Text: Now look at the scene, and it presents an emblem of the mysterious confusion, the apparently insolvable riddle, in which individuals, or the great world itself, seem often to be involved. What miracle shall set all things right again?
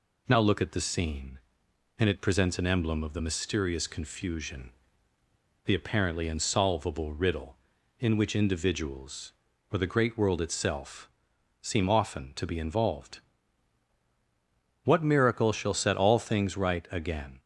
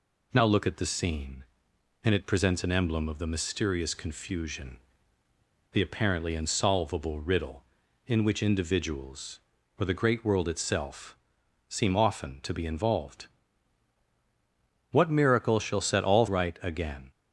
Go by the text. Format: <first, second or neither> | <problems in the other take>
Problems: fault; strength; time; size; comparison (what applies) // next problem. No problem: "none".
first | skips "things"; at 16.2 s